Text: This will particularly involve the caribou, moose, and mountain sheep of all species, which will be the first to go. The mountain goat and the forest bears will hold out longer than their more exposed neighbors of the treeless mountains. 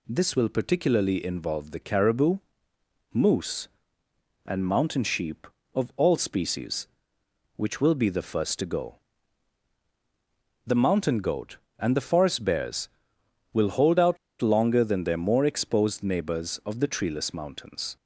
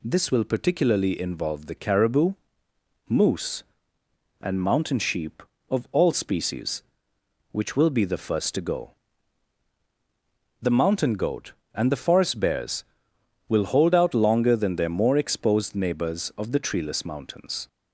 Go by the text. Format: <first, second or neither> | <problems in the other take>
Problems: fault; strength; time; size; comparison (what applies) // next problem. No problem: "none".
second | pauses between "out" and "longer"; slight; at 14.1 s; 0.24 s long